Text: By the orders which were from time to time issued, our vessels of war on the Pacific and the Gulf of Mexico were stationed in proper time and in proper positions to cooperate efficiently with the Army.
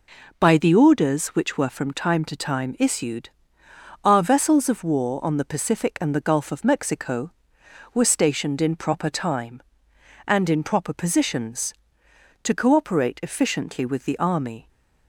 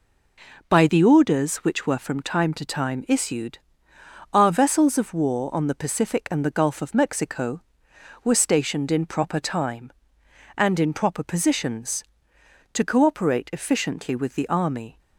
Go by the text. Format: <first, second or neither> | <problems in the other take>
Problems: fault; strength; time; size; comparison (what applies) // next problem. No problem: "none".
neither | none